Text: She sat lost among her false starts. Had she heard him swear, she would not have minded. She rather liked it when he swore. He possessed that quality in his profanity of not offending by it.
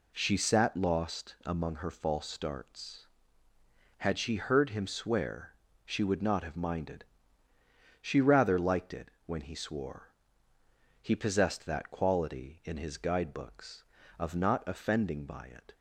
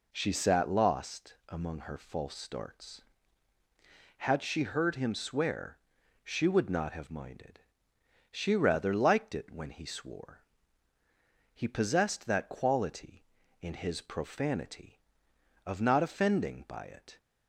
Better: second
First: pauses between "it" and "when"; slight; at 9.0 s; 0.16 s long // says "guidebooks" for "profanity"; at 12.9 s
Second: none

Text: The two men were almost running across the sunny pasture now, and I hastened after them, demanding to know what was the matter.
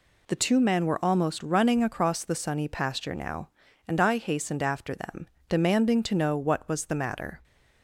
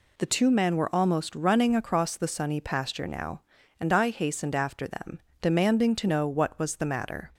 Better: neither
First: none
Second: none

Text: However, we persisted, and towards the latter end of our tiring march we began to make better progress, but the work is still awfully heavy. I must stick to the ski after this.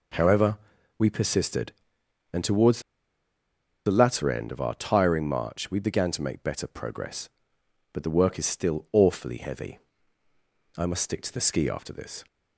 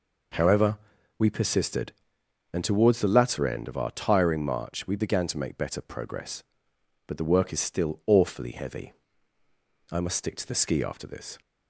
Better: second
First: pauses between "towards" and "the"; at 2.8 s; 1.0 s long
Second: none

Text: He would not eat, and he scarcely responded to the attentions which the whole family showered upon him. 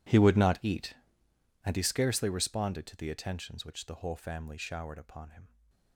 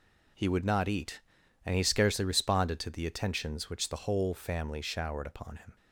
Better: second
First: gets quieter; strong; throughout; 21.5 dB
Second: none

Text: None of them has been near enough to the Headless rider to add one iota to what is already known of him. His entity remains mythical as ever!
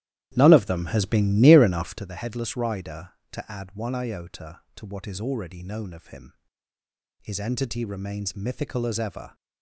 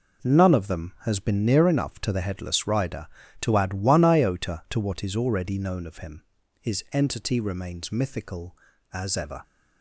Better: second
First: starts louder than the rest; strong; until 2.1 s; 12.5 dB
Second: none

